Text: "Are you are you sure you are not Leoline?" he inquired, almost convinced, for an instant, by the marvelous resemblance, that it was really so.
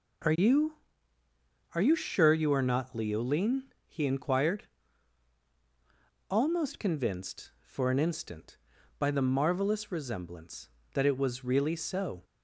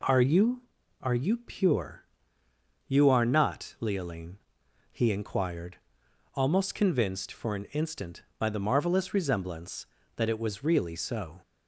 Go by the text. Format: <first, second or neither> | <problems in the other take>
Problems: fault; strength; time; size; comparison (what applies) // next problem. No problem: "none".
first | says "pure" for "sure"; at 1.3 s